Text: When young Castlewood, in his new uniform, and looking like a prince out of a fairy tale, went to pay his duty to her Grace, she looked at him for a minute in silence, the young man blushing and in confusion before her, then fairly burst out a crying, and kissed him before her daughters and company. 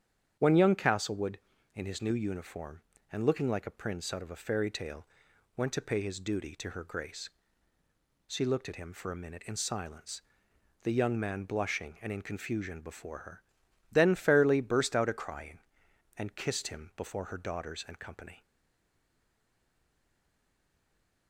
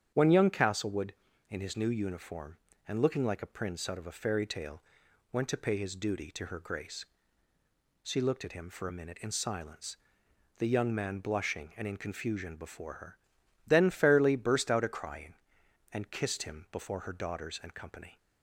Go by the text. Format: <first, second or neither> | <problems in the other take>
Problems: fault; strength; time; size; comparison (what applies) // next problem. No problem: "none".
second | starts louder than the rest; strong; until 1.4 s; 8.5 dB; strong in the second // stays silent after the last word; strong; from 18.4 s on; 2.8 s long